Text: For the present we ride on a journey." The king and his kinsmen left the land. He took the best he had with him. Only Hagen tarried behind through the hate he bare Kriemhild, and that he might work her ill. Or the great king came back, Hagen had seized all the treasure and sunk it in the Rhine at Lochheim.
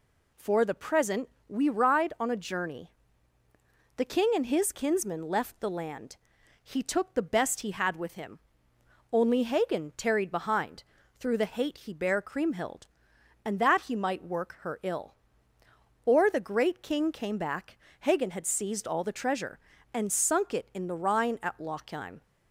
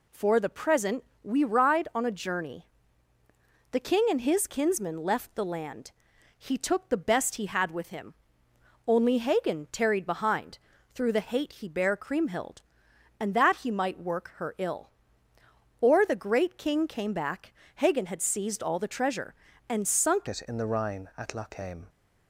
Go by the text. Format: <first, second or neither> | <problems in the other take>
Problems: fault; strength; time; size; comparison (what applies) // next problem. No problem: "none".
first | pauses between "present" and "we"; slight; at 1.0 s; 0.18 s long; slight in the first // pauses between "behind" and "through"; slight; at 10.5 s; 0.36 s long; slight in the first // changes voice at "it"; from 20.2 s on; 1.6 s long